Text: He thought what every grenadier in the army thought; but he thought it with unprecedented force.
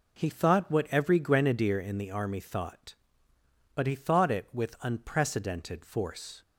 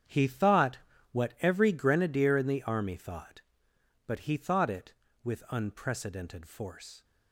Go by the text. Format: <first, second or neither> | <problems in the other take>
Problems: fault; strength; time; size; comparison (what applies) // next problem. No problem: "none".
first | gets quieter; strong; throughout; 14 dB // pauses between "thought" and "what"; slight; at 0.7 s; 0.34 s long